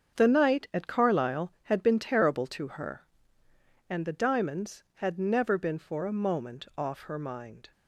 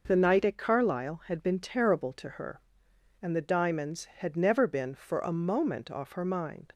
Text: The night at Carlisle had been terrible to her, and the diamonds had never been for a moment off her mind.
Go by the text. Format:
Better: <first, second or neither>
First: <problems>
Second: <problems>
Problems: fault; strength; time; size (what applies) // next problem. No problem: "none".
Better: second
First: gets quieter; strong; throughout; 9 dB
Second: none